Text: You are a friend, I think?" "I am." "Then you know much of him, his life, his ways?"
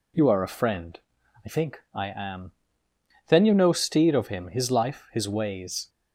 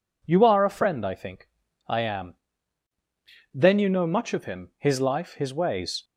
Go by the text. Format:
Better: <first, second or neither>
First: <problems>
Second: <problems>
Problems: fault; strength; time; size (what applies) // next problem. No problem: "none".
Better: second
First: says "steed" for "much"; at 3.7 s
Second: none